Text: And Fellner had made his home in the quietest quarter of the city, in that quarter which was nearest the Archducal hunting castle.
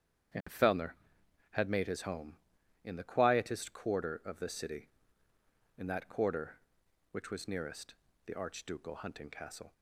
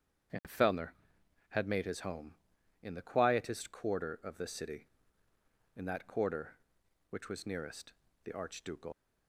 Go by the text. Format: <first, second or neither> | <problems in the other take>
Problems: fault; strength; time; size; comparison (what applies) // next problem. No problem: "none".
first | starts louder than the rest; strong; until 1.9 s; 8 dB; strong in the first // pauses between "nearest" and "the"; slight; at 7.9 s; 0.32 s long; slight in the first // stops before "hunting castle"; at 8.9 s